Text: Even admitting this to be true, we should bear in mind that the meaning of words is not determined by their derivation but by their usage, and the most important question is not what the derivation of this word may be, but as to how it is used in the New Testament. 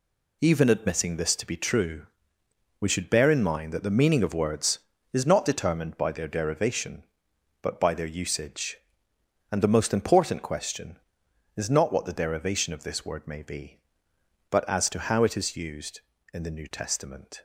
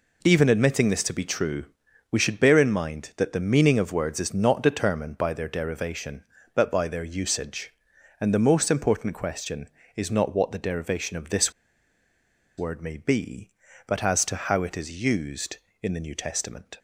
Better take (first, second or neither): first